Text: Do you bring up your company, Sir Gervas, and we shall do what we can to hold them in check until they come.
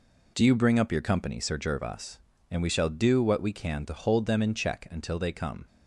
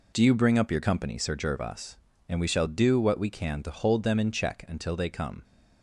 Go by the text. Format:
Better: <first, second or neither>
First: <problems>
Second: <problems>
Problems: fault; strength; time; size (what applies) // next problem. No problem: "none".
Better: neither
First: none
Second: none